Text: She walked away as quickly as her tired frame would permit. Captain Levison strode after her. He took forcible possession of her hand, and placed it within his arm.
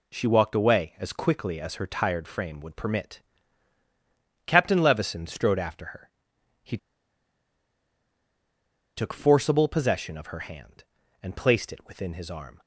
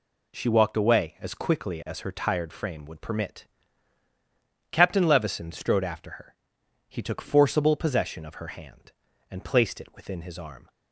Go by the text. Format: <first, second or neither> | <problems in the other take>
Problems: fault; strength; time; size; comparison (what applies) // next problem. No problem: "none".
second | pauses between "He" and "took"; strong; at 6.7 s; 2.1 s long